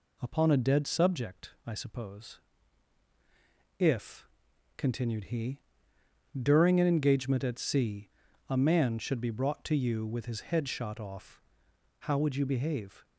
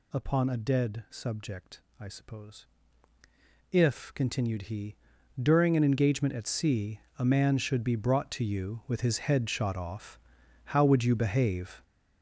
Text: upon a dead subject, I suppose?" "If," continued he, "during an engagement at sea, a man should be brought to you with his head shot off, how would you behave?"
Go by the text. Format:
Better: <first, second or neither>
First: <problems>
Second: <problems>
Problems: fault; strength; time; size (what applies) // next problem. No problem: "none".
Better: first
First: none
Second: gets louder; strong; throughout; 9.5 dB